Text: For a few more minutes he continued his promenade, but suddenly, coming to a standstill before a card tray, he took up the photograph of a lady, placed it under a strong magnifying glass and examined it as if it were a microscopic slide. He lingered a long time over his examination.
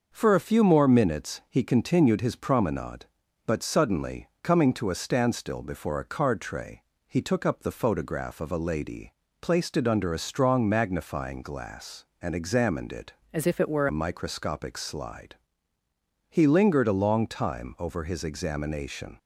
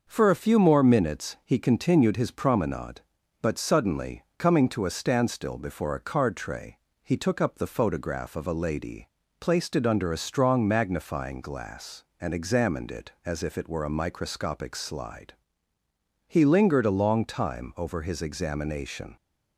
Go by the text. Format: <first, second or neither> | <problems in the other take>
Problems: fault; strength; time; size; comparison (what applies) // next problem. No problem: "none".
second | starts louder than the rest; until 1.1 s; 6.5 dB; also in the second // changes voice from "as" to "were"; from 13.3 to 13.8 s; 0.5 s long